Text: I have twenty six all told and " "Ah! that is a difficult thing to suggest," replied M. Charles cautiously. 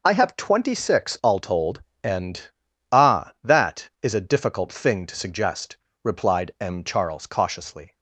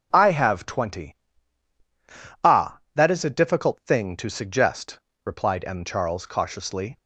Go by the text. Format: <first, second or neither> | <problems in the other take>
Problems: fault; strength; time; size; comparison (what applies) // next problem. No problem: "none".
first | starts louder than the rest; until 1.1 s; 7 dB // skips "six all told and"; at 1.4 s